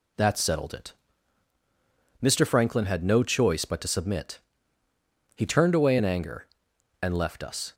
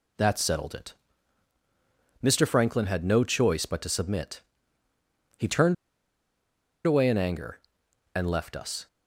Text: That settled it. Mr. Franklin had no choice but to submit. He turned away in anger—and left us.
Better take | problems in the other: first | pauses between "turned" and "away"; at 5.7 s; 1.1 s long

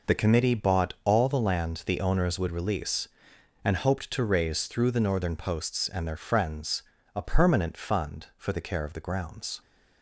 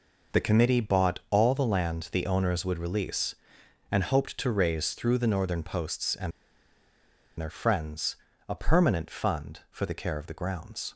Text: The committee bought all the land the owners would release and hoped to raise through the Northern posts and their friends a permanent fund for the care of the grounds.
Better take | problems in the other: first | pauses between "and" and "their"; at 6.3 s; 1.0 s long // pauses between "friends" and "a"; slight; at 8.1 s; 0.34 s long; slight in the first

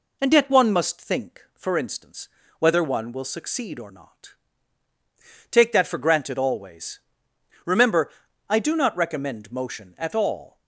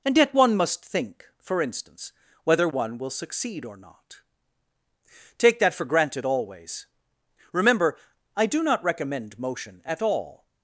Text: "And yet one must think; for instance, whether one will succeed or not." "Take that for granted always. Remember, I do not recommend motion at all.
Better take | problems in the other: neither | none

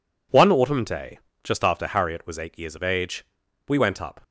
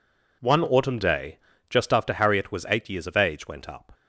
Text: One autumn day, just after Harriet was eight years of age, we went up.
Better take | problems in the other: first | skips "we"; at 3.4 s

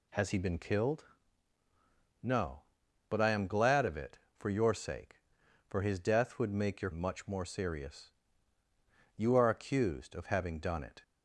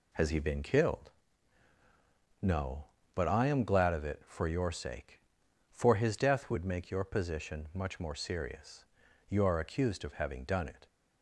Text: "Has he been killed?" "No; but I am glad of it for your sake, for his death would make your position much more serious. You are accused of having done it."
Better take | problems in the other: second | skips "position"; at 6.9 s

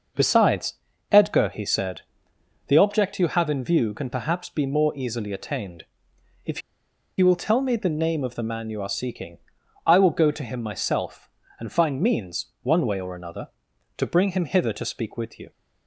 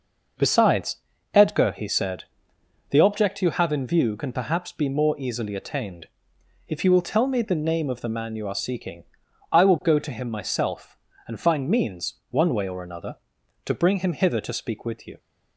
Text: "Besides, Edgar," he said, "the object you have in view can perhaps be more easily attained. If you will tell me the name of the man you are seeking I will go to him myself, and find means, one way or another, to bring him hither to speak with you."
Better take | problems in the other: second | pauses between "If" and "you"; noticeable; at 6.6 s; 0.57 s long // pauses between "seeking" and "I"; noticeable; at 9.3 s; 0.48 s long; noticeable in the second

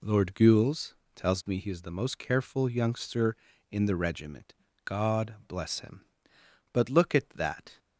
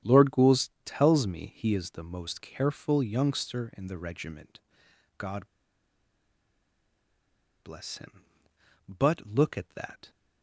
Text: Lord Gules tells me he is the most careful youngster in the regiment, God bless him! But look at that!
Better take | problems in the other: first | starts louder than the rest; strong; until 1.2 s; 9.5 dB // pauses between "Gules" and "tells"; slight; at 0.6 s; 0.16 s long; slight in the first // pauses between "God" and "bless"; strong; at 5.4 s; 2.1 s long

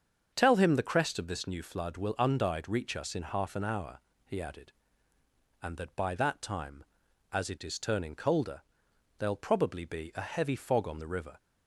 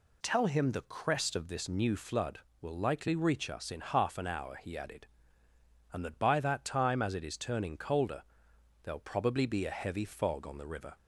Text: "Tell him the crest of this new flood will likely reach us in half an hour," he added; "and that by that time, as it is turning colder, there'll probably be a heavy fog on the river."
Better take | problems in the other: second | starts louder than the rest; strong; until 1.3 s; 7 dB // says "undyed" for "likely"; at 2.1 s

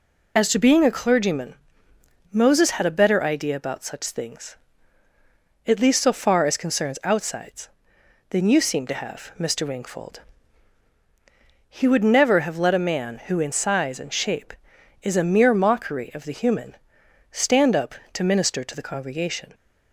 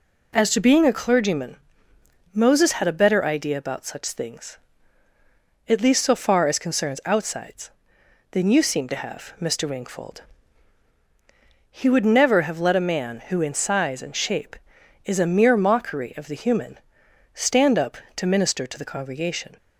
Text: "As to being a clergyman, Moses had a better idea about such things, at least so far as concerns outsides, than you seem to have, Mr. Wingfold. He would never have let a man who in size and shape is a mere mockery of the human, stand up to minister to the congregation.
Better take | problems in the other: second | loses the start of "As"; at 0.3 s; 45 ms

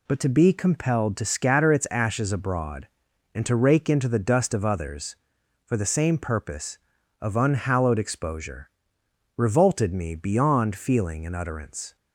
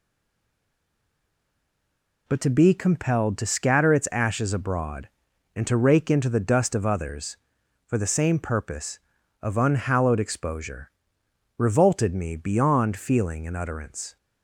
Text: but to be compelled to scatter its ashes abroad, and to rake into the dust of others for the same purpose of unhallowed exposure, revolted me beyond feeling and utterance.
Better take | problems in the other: first | stays silent before the first word; until 2.2 s; 2.2 s long

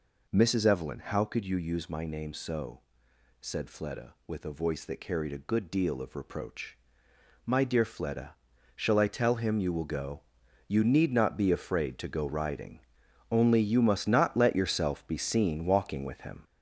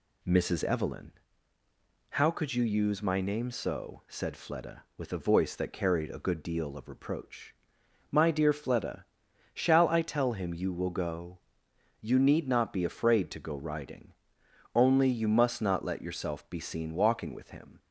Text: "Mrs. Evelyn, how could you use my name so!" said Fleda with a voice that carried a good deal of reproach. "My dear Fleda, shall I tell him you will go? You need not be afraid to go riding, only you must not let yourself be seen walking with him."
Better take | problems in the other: second | gets louder; noticeable; throughout; 5 dB

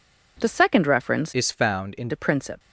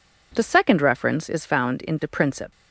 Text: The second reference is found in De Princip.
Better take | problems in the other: second | changes voice from "is" to "in"; from 1.3 to 2.0 s; 0.7 s long

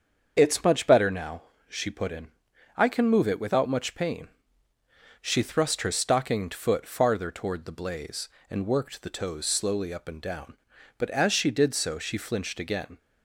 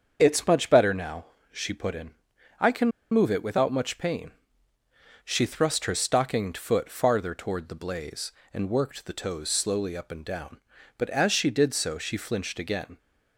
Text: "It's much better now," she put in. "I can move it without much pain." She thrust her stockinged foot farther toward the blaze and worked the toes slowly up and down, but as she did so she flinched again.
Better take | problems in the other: first | starts louder than the rest; until 1.2 s; 7 dB; also in the first // pauses between "can" and "move"; slight; at 2.9 s; 0.22 s long

